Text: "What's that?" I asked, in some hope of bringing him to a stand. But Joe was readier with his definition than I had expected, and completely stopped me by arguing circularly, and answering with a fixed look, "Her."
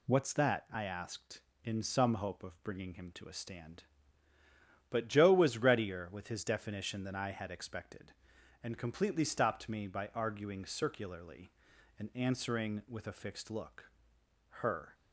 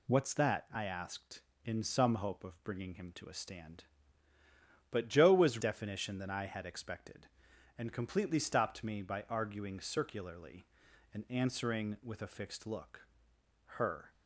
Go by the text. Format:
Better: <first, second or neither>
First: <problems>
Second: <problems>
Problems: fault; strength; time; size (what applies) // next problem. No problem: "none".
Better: first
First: none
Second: skips "readier with his"; at 5.5 s